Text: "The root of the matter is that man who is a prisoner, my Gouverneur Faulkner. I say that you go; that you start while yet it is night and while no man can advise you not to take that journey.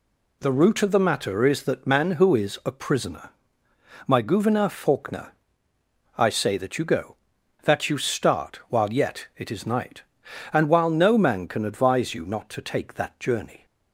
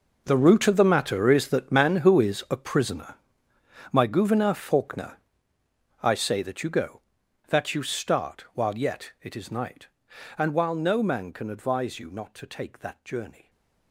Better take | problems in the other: first | gets quieter; strong; throughout; 16 dB

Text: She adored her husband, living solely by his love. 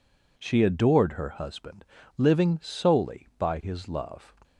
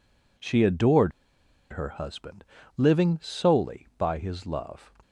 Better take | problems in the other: first | pauses between "adored" and "her"; noticeable; at 1.1 s; 0.60 s long

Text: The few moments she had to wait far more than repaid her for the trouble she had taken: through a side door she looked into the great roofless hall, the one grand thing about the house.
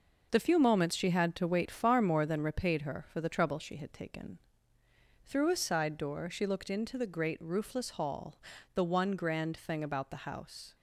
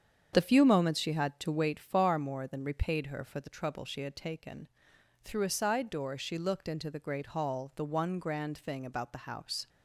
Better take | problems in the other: first | starts louder than the rest; strong; until 1.3 s; 8 dB // skips "roofless"; at 7.2 s

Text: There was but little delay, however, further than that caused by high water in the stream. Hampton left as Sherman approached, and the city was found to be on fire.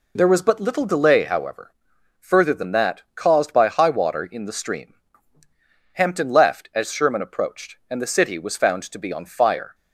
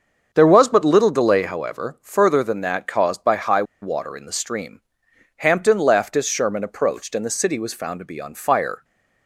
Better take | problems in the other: first | starts louder than the rest; until 1.3 s; 7 dB // pauses between "high" and "water"; slight; at 3.6 s; 0.18 s long

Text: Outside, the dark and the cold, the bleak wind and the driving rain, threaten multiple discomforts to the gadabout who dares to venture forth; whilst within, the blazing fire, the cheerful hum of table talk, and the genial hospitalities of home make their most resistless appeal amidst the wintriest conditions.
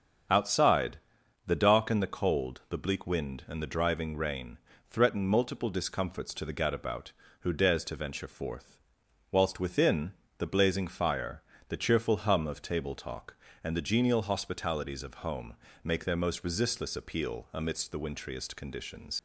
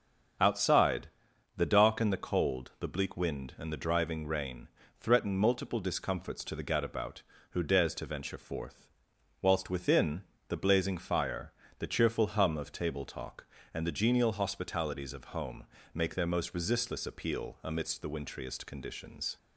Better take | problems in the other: second | starts louder than the rest; strong; until 1.7 s; 7.5 dB; strong in the second // pauses between "home" and "make"; slight; at 15.5 s; 0.26 s long; slight in the second // leaves "conditions" unfinished; at 19.1 s; 80 ms

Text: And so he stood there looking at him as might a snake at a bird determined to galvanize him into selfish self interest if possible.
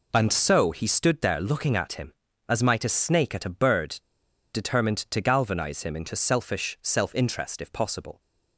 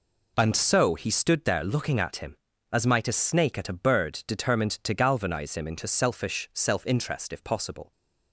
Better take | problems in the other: second | pauses between "bird" and "determined"; noticeable; at 4.0 s; 0.51 s long

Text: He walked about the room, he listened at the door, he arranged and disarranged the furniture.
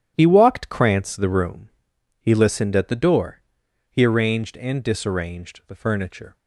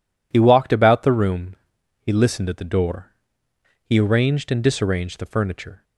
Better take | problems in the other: second | starts louder than the rest; strong; until 1.1 s; 10 dB // says "krantz" for "about"; at 0.6 s

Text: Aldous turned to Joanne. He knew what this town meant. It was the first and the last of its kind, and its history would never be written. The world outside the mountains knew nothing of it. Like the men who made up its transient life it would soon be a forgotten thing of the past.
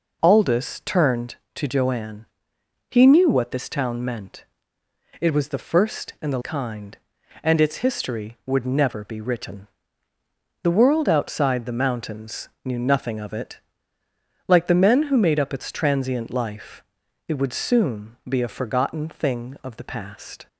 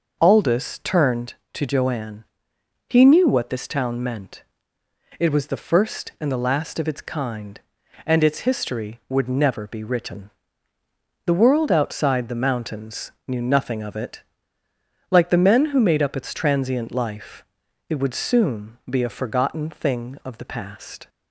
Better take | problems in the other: second | skips "last of its"; at 6.4 s // pauses between "mountains" and "knew"; slight; at 12.4 s; 0.16 s long; slight in the second // pauses between "life" and "it"; noticeable; at 16.8 s; 0.46 s long; noticeable in the second

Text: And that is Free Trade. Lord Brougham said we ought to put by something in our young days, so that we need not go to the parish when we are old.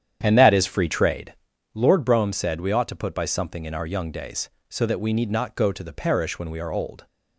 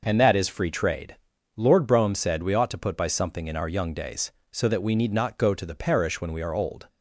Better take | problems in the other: second | starts louder than the rest; strong; until 1.5 s; 9 dB

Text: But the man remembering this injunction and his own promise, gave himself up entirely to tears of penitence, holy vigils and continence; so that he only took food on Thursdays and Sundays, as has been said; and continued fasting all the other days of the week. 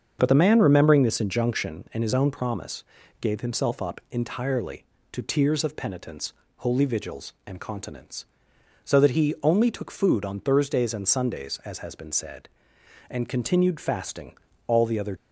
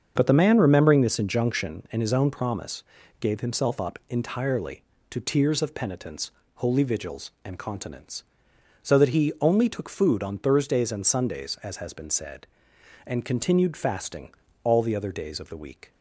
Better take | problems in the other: second | starts louder than the rest; until 1.2 s; 7 dB; also in the second // pauses between "fasting" and "all"; slight; at 14.3 s; 0.30 s long; slight in the second // stops before "days of the week"; at 15.1 s

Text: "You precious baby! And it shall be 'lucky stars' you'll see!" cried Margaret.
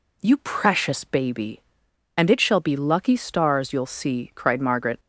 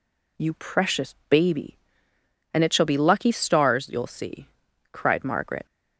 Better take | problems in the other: neither | none

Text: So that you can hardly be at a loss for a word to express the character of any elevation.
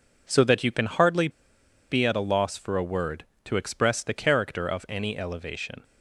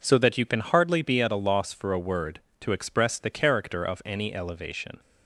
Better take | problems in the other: second | pauses between "hardly" and "be"; noticeable; at 1.2 s; 0.61 s long

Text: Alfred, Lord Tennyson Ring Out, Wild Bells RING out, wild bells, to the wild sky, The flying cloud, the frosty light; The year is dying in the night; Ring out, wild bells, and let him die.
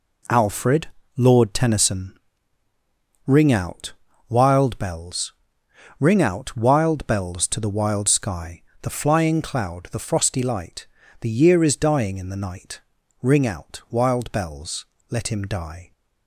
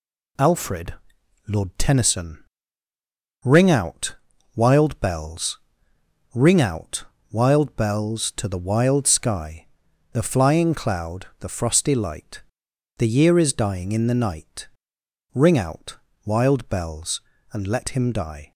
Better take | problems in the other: second | pauses between "Tennyson" and "Ring"; at 2.1 s; 1.0 s long; also in the second // pauses between "Bells" and "RING"; noticeable; at 5.3 s; 0.66 s long; noticeable in the second // skips "and"; at 14.9 s

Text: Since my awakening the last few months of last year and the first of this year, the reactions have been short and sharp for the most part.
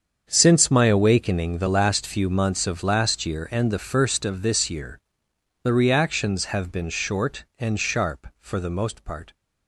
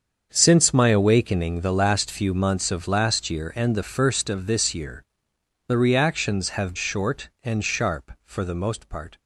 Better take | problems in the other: first | starts louder than the rest; until 1.3 s; 7 dB; strong in the first // skips "been"; at 6.7 s

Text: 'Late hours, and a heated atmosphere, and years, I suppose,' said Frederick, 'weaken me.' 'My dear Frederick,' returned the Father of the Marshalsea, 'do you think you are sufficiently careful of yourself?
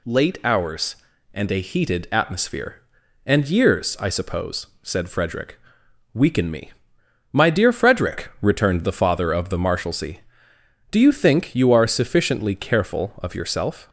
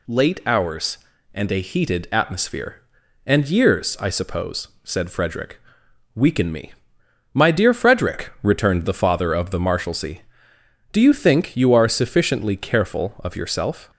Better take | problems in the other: neither | none

